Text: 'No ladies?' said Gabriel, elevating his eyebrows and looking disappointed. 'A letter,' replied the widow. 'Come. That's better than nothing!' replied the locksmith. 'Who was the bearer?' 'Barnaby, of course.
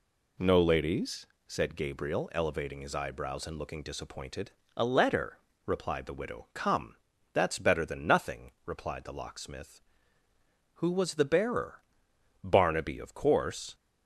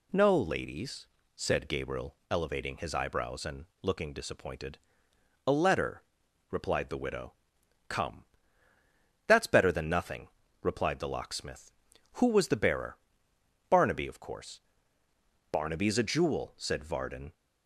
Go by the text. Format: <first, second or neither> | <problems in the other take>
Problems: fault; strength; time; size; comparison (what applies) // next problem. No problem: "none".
first | pauses between "and" and "looking"; slight; at 3.6 s; 0.16 s long // goes on to say "Barnaby's a jewel said Varden"; strong; from 15.5 s on; 1.8 s long